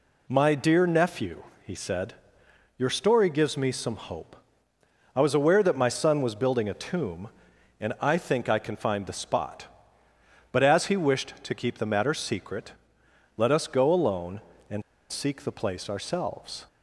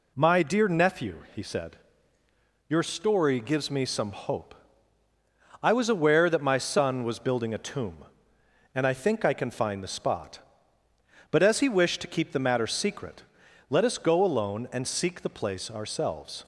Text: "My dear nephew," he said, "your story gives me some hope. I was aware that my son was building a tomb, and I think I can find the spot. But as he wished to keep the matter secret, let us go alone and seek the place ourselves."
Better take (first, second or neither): second